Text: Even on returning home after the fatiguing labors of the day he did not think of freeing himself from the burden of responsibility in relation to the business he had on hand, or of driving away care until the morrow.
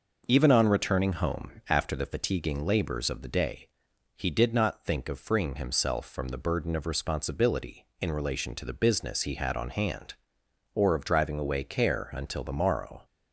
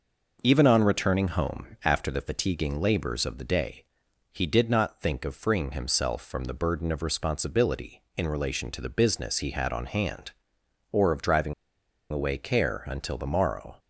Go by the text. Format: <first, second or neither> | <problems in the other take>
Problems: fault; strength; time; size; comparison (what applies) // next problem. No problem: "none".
first | pauses between "day" and "he"; noticeable; at 3.8 s; 0.48 s long; noticeable in the first // pauses between "driving" and "away"; noticeable; at 11.5 s; 0.58 s long